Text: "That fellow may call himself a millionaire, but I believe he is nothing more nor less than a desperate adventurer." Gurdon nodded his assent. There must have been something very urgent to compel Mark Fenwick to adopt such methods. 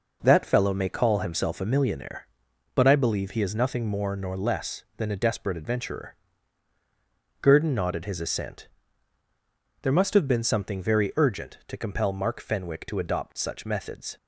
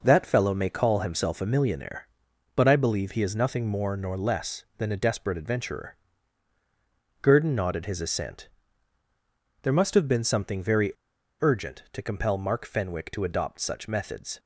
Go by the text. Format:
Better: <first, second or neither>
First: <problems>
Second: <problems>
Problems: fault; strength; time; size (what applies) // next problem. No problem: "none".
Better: first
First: none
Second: pauses between "very" and "urgent"; noticeable; at 10.9 s; 0.50 s long